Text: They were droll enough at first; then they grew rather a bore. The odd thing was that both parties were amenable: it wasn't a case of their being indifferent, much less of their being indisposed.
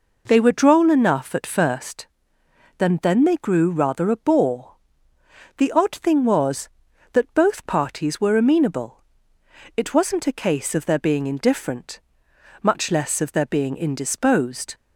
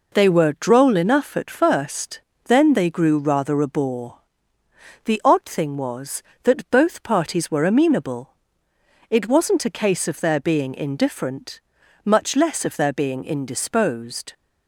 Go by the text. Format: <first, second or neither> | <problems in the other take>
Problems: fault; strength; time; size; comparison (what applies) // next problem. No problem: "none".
second | says "then" twice; at 3.0 s